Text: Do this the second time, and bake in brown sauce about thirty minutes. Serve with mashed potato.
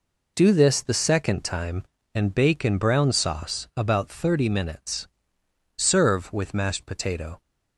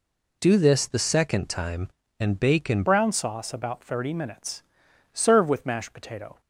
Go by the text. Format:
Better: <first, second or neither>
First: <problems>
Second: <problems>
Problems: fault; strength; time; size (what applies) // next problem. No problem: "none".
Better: first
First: none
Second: changes voice at "brown"; from 2.8 s on; 3.5 s long